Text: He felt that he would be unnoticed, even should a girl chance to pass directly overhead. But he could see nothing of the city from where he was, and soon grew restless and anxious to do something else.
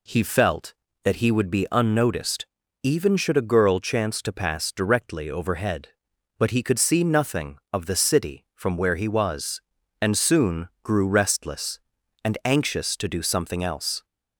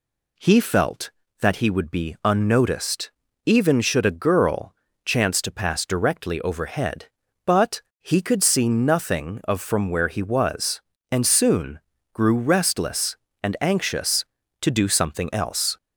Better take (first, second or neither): first